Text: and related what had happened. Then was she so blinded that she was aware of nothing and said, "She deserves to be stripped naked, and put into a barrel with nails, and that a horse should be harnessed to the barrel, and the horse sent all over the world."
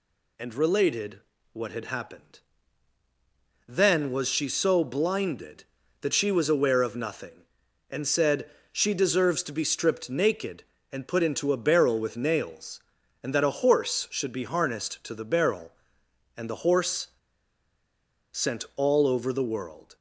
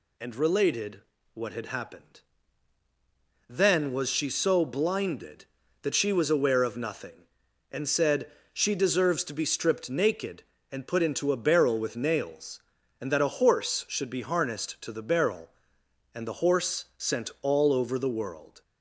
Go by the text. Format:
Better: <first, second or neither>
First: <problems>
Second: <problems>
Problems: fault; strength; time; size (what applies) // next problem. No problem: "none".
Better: second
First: pauses between "related" and "what"; slight; at 1.2 s; 0.32 s long // pauses between "horse" and "sent"; at 17.0 s; 1.2 s long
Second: pauses between "related" and "what"; slight; at 1.0 s; 0.32 s long